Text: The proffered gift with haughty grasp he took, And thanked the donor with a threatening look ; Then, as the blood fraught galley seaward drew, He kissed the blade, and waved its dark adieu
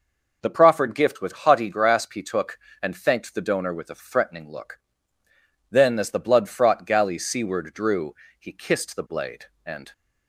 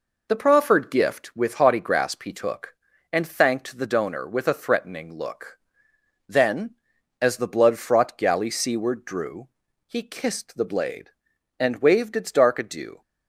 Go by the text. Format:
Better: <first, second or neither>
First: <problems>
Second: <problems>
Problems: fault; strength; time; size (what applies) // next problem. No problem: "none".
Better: second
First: stops before "waved its dark adieu"; at 9.9 s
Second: none